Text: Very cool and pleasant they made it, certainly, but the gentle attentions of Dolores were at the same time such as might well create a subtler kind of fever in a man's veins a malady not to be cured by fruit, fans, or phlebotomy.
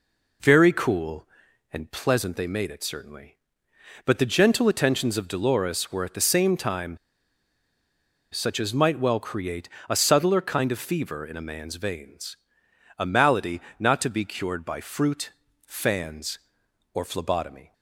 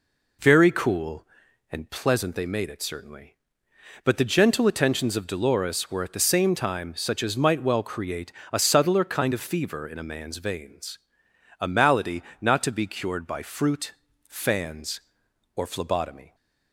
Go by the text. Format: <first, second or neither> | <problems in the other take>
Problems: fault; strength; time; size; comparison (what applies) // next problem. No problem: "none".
second | pauses between "time" and "such"; strong; at 6.9 s; 1.3 s long // pauses between "create" and "a"; slight; at 9.6 s; 0.22 s long; slight in the second // pauses between "veins" and "a"; noticeable; at 12.3 s; 0.60 s long; noticeable in the second // pauses between "malady" and "not"; slight; at 13.5 s; 0.18 s long; slight in the second